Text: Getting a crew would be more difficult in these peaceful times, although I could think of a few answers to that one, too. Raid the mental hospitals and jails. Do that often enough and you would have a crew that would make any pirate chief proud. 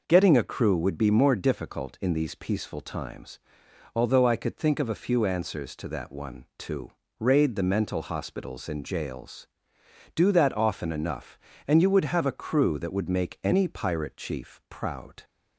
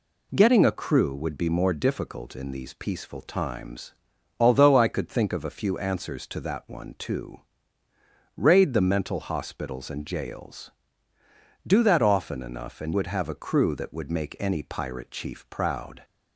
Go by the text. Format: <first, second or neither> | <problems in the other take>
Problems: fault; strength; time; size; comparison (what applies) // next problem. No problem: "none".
first | skips "you"; at 12.9 s